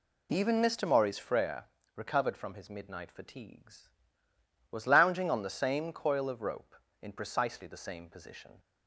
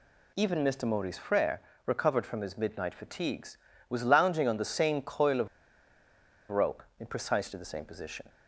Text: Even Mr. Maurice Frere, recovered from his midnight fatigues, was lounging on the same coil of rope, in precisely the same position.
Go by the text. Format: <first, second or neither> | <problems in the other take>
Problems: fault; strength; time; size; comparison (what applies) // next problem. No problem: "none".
first | pauses between "of" and "rope"; at 5.4 s; 1.0 s long